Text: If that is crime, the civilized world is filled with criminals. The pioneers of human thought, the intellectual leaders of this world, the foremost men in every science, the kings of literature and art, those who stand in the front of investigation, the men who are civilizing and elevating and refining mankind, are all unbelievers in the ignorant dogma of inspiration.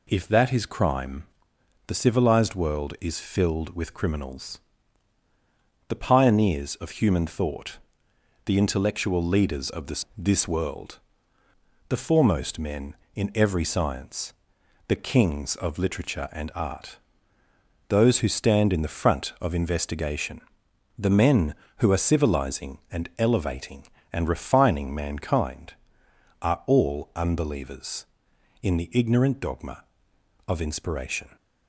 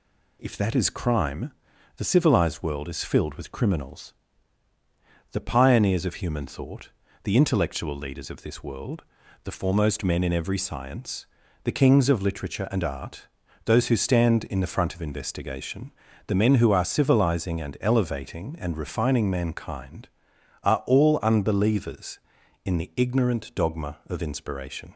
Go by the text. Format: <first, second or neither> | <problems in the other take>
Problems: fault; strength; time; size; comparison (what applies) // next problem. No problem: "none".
second | says "this" twice; at 10.1 s